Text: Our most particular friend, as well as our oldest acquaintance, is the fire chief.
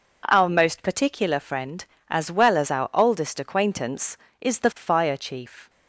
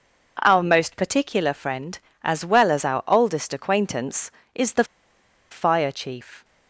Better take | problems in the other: first | pauses between "the" and "fire"; noticeable; at 4.8 s; 0.66 s long

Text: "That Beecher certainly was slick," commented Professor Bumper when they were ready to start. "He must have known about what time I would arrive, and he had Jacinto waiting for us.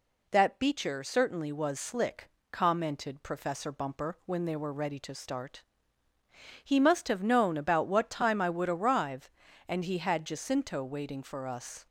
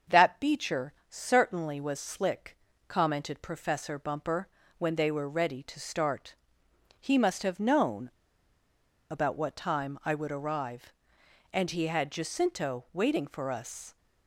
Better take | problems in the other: first | starts louder than the rest; until 1.2 s; 6.5 dB // pauses between "Beecher" and "certainly"; slight; at 0.9 s; 0.16 s long // pauses between "Bumper" and "when"; slight; at 4.4 s; 0.30 s long // pauses between "known" and "about"; at 8.1 s; 1.0 s long

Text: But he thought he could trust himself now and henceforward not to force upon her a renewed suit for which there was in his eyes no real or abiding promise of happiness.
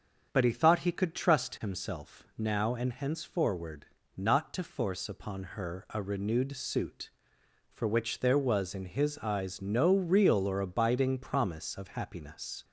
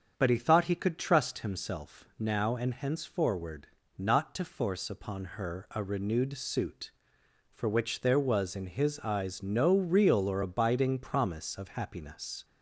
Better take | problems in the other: neither | starts louder than the rest; the same in both // pauses between "henceforward" and "not"; slight; the same in both

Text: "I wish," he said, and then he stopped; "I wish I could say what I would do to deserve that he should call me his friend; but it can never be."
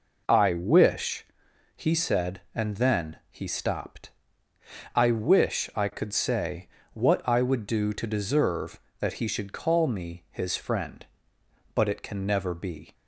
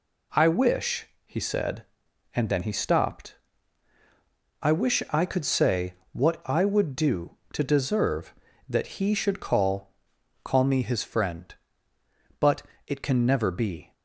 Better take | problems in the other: first | pauses between "say" and "what"; slight; at 5.9 s; 0.18 s long; slight in the first // says "call" twice; at 10.4 s // pauses between "but" and "it"; slight; at 12.6 s; 0.24 s long

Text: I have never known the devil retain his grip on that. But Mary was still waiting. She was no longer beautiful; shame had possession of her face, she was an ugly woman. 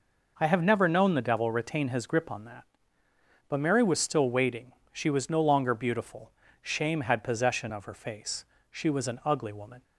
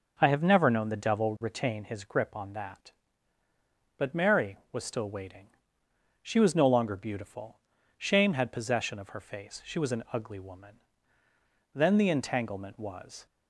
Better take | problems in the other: first | goes on to say "Then the entanglement was"; from 11.7 s on; 1.5 s long

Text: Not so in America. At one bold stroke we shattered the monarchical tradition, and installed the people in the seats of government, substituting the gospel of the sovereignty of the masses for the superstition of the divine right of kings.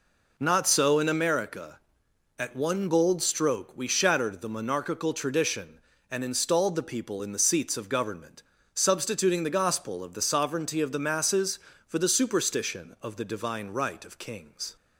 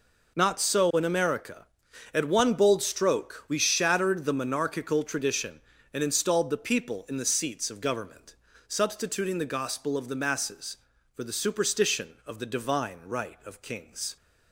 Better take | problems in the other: first | skips "sovereignty of the"; at 10.1 s

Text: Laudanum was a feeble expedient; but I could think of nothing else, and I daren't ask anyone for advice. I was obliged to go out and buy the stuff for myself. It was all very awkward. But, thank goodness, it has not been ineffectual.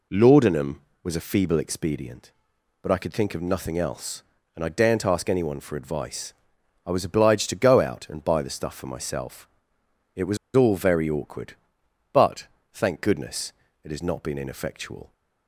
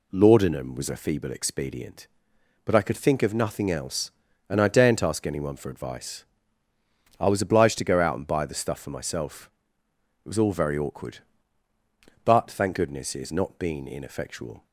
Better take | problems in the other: second | pauses between "was" and "all"; slight; at 10.3 s; 0.17 s long

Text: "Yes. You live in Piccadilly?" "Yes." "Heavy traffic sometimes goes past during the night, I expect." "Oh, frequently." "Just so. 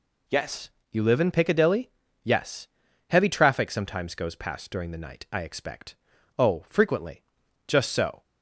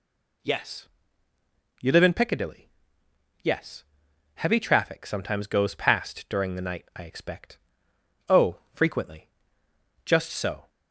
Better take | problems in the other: neither | none

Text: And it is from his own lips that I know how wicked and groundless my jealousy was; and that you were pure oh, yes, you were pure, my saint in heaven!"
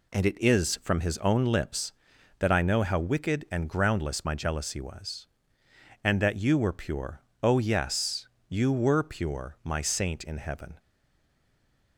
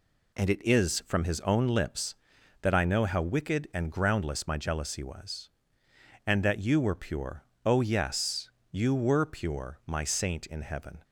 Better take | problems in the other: second | pauses between "pure" and "oh"; slight; at 7.2 s; 0.20 s long; slight in the second // stays silent after the last word; noticeable; from 10.7 s on; 1.2 s long

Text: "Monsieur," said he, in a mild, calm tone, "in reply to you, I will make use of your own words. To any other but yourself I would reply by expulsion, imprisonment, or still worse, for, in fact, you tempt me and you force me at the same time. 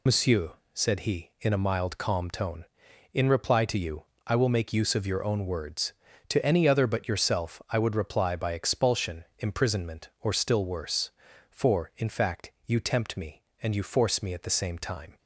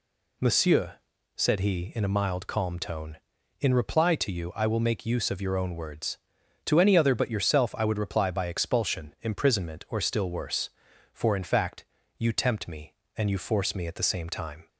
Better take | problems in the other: second | loses the start of "Monsieur"; at 0.0 s; 60 ms

